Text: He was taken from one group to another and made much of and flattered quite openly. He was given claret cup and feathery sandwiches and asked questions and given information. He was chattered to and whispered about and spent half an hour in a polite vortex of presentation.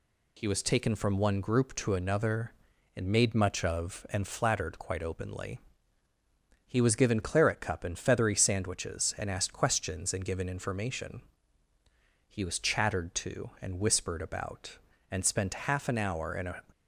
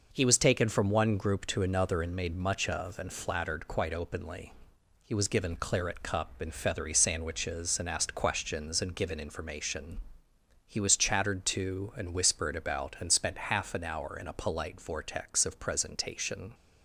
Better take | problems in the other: second | stops before "polite vortex of presentation"; at 16.7 s

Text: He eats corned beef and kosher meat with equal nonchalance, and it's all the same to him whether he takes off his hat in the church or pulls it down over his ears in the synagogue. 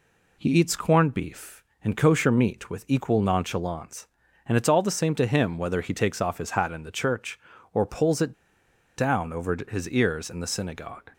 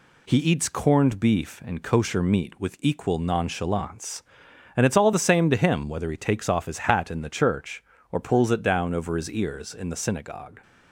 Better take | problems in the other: second | pauses between "it" and "down"; noticeable; at 8.3 s; 0.63 s long

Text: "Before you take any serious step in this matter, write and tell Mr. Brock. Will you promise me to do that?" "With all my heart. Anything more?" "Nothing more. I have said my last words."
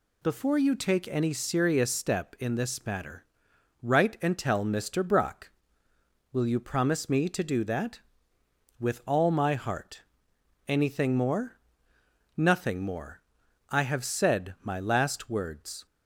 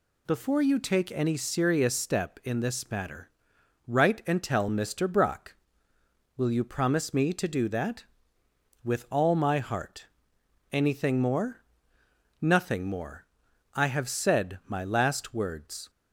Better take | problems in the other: neither | none

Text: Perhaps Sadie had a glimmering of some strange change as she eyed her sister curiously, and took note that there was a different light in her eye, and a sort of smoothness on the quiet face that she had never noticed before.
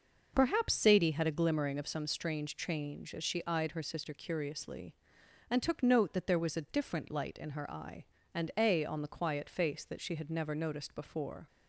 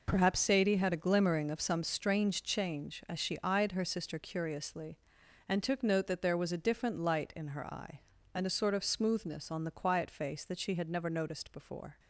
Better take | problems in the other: second | skips "sort of smoothness"; at 8.8 s

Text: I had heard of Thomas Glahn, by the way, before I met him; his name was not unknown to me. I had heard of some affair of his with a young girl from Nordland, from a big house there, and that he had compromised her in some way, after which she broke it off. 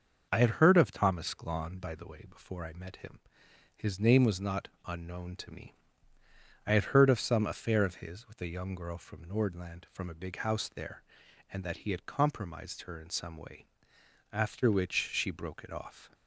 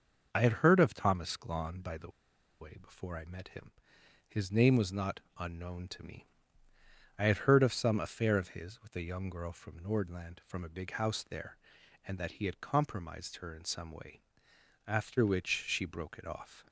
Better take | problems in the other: first | starts louder than the rest; until 1.3 s; 6.5 dB; also in the first // pauses between "the" and "way"; noticeable; at 2.0 s; 0.51 s long // pauses between "not" and "unknown"; slight; at 5.2 s; 0.16 s long; slight in the first

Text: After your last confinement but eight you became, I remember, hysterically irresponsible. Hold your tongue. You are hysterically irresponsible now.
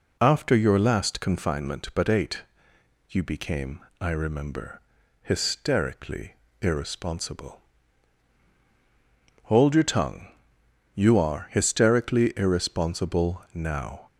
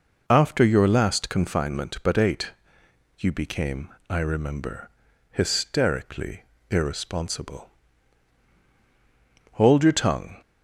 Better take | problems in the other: first | pauses between "eight" and "you"; noticeable; at 2.5 s; 0.68 s long; noticeable in the first // pauses between "hysterically" and "irresponsible"; slight; at 6.4 s; 0.26 s long; slight in the first // stops before "You are hysterically irresponsible now"; at 10.4 s

